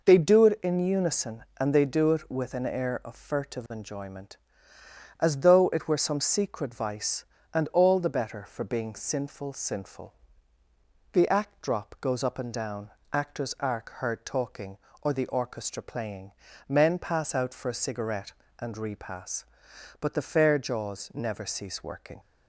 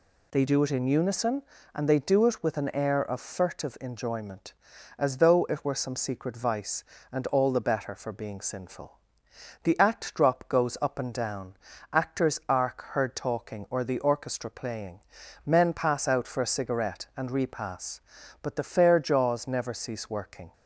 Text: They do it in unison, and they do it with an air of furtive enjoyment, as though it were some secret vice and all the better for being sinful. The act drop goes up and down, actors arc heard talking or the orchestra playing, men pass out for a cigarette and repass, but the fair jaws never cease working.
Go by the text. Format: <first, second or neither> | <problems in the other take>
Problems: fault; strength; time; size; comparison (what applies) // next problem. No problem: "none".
second | says "sinful" twice; at 9.5 s